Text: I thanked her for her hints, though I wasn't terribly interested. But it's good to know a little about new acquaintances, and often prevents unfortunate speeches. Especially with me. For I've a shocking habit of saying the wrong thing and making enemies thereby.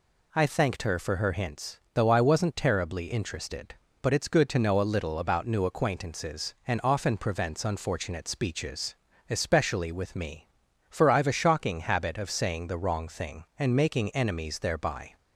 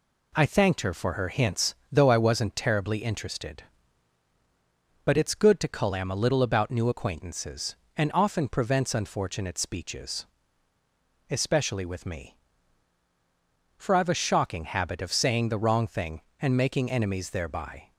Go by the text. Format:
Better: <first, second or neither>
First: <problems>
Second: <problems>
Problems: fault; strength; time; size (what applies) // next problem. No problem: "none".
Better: first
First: none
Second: says "calam" for "know"; at 5.6 s